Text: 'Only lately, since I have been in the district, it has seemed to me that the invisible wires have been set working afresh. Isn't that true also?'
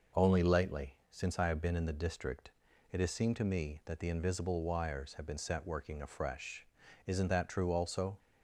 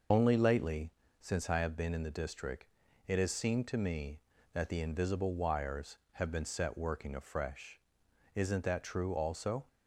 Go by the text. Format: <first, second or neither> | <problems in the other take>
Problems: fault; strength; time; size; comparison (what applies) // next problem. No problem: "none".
first | loses the start of "Only"; at 0.1 s; 75 ms